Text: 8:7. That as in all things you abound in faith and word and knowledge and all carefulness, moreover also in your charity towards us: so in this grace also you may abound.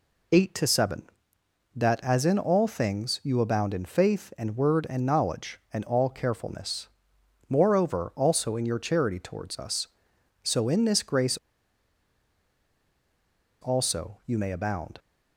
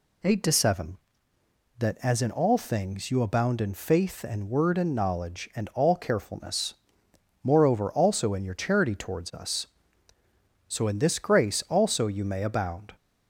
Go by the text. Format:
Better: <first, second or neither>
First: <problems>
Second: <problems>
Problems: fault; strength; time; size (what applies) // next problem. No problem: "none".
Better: second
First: pauses between "grace" and "also"; strong; at 11.3 s; 2.2 s long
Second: none